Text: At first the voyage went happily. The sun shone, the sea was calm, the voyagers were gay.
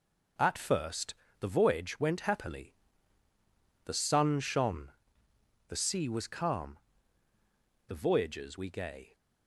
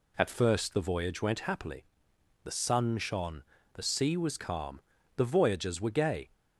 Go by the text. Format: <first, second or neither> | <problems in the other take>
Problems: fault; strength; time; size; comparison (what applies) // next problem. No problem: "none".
second | pauses between "first" and "the"; slight; at 1.1 s; 0.26 s long // says "we" for "were"; at 8.5 s